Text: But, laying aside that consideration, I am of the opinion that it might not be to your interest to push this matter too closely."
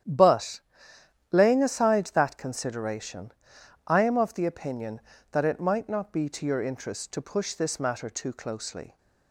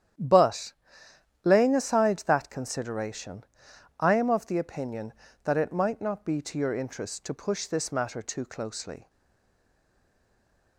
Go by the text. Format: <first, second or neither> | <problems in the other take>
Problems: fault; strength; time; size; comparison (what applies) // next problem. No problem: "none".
first | starts louder than the rest; strong; until 1.9 s; 10 dB; strong in the first // stays silent after the last word; noticeable; from 9.0 s on; 1.7 s long